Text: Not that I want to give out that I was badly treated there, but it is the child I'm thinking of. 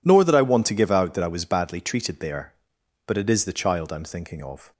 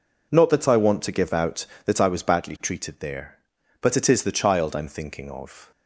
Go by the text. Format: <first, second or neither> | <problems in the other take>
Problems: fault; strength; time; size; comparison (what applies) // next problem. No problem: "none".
second | says "Nor" for "Not"; at 0.0 s